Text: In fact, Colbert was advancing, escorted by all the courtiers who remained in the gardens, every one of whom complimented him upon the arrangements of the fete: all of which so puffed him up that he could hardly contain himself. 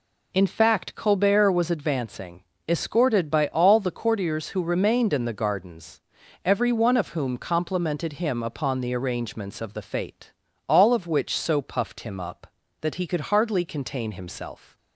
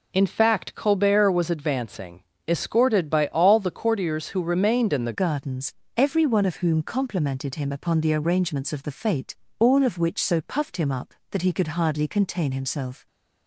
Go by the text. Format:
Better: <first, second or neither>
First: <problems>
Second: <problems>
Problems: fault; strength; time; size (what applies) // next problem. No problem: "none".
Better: first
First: none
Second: changes voice at "gardens"; from 5.1 s on; 7.9 s long